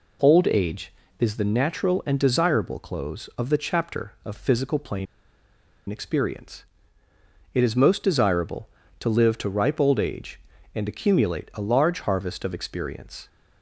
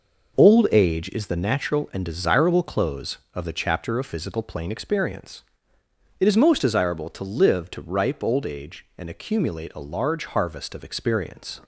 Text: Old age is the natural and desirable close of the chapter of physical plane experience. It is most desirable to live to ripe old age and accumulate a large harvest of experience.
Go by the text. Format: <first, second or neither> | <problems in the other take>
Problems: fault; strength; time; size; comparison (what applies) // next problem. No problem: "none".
second | pauses between "plane" and "experience"; noticeable; at 5.0 s; 0.84 s long